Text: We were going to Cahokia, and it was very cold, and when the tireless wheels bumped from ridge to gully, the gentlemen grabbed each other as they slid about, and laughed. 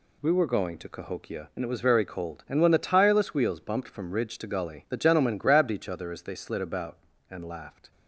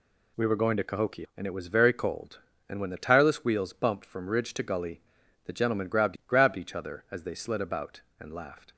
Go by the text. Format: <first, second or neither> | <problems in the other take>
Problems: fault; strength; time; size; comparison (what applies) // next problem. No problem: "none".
first | says "grabbed" twice; at 6.2 s